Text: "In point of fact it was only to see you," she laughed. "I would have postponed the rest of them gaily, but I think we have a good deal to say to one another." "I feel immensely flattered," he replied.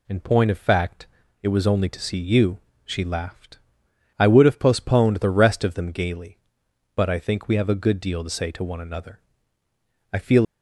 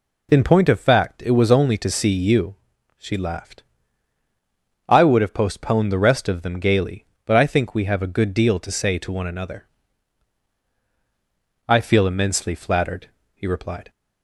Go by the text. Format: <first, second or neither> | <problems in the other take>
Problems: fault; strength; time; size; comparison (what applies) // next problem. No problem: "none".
second | pauses between "fact" and "it"; slight; at 1.0 s; 0.34 s long // stops before "immensely flattered he replied"; at 10.4 s